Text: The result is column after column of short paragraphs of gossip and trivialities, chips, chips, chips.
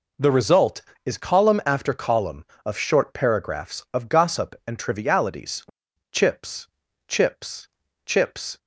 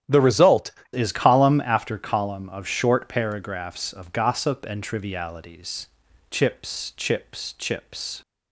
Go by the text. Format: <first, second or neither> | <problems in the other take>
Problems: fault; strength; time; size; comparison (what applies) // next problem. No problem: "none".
first | starts louder than the rest; strong; until 1.2 s; 10 dB // changes voice at "is"; from 0.9 s on; 7.3 s long